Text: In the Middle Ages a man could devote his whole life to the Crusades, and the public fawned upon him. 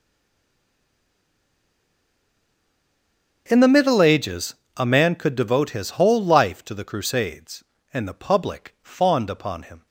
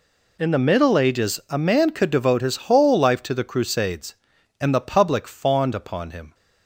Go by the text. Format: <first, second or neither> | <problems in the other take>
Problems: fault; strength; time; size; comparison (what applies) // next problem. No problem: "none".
second | stays silent before the first word; strong; until 3.4 s; 3.4 s long // starts louder than the rest; until 4.4 s; 7 dB // pauses between "Ages" and "a"; slight; at 4.5 s; 0.20 s long